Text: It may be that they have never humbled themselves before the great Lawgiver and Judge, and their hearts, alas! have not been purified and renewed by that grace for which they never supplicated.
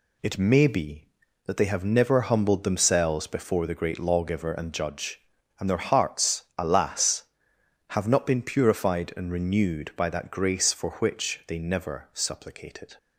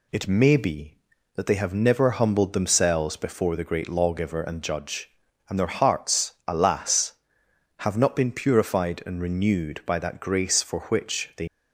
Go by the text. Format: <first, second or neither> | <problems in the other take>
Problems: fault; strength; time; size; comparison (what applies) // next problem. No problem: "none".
first | stops before "never supplicated"; at 11.4 s